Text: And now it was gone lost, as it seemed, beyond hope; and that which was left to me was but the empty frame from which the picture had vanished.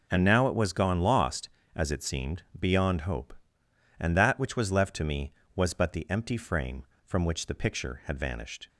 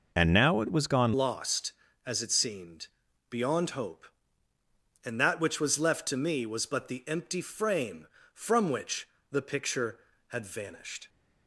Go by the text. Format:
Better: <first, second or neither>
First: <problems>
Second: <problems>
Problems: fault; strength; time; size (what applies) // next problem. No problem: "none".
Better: first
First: none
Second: changes voice at "lost"; from 1.1 s on; 9.9 s long // pauses between "which" and "the"; slight; at 9.0 s; 0.22 s long